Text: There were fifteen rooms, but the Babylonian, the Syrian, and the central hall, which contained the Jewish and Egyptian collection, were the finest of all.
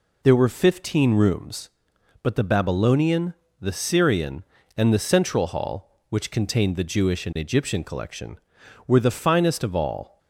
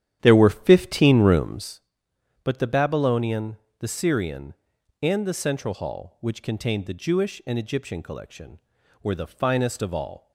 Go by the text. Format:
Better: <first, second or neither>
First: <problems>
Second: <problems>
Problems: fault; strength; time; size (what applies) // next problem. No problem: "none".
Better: first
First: none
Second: starts louder than the rest; strong; until 1.8 s; 10.5 dB